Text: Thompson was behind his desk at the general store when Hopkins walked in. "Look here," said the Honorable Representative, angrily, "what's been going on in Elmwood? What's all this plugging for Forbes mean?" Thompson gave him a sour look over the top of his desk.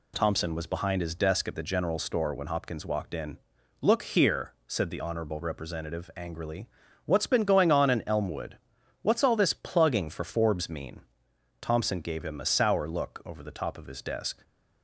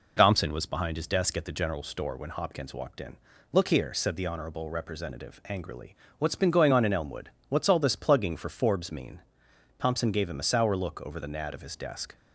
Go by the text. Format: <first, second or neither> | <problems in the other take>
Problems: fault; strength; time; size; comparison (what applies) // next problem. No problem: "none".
first | says "nad" for "top"; at 11.2 s